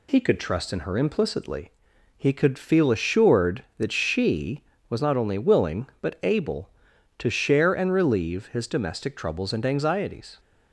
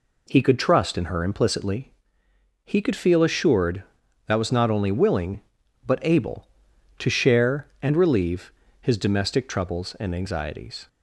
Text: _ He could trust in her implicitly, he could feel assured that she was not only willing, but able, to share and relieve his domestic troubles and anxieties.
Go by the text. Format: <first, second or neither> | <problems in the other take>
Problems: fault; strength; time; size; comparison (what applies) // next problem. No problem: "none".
first | skips "she"; at 4.3 s // pauses between "relieve" and "his"; slight; at 8.5 s; 0.30 s long